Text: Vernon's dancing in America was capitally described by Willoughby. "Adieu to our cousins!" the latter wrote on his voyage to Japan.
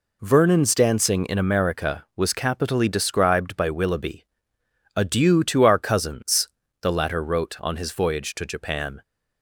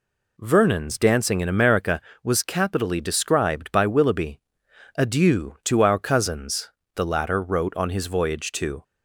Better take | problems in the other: first | stops before "Japan"; at 8.8 s

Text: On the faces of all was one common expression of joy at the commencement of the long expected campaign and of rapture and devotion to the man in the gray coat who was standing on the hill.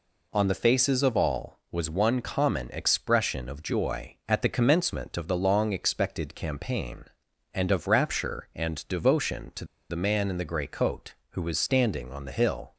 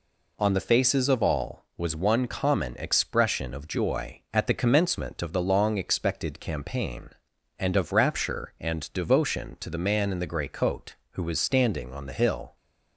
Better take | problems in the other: second | pauses between "to" and "the"; slight; at 9.6 s; 0.24 s long

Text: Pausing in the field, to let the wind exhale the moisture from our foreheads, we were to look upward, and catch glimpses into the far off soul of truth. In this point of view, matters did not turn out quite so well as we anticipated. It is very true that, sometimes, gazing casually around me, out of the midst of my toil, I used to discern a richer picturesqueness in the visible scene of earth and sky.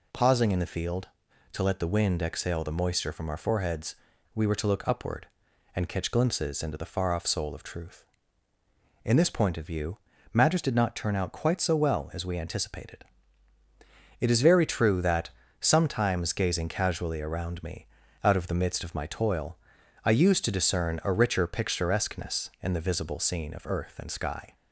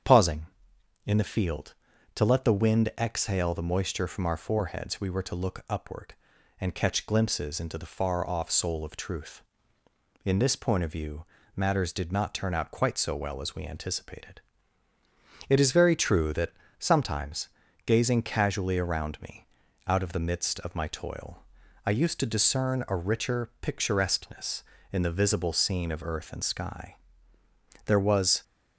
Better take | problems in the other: first | starts louder than the rest; strong; until 1.6 s; 8 dB // goes on to say "There was"; from 27.8 s on; 0.58 s long

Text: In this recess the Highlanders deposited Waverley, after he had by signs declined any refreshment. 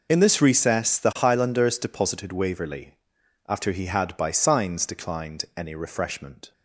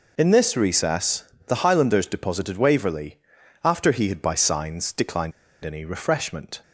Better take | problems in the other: first | pauses between "recess" and "the"; slight; at 1.2 s; 0.24 s long // pauses between "declined" and "any"; slight; at 5.3 s; 0.32 s long

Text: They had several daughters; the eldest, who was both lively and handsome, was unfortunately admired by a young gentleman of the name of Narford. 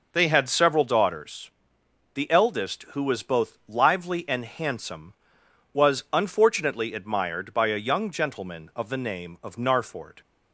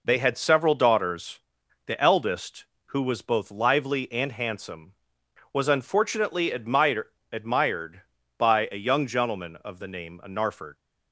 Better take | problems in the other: first | says "admired" twice; at 7.3 s

